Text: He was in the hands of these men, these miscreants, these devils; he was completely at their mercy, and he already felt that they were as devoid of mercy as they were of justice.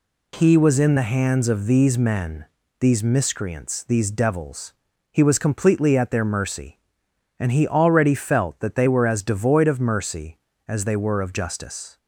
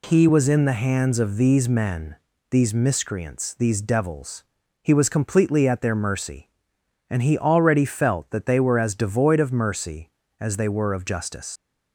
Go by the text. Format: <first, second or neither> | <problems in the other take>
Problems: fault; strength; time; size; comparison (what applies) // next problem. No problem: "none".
first | leaves "justice" unfinished; at 11.5 s; 135 ms